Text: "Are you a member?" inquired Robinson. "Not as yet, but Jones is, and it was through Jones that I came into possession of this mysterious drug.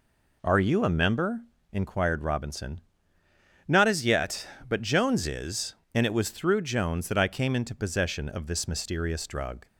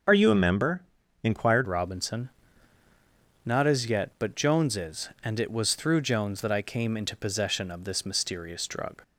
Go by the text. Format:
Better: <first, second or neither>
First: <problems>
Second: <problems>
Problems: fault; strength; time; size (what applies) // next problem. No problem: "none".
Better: first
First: none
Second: starts louder than the rest; until 1.4 s; 6.5 dB // changes voice at "Robinson"; from 1.6 s on; 7.4 s long